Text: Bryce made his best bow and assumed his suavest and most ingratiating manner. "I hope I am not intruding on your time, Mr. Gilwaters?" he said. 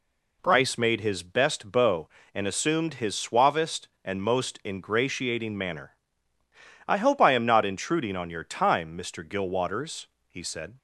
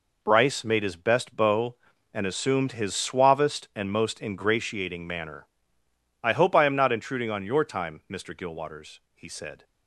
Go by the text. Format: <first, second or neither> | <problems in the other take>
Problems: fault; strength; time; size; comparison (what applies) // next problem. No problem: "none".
neither | none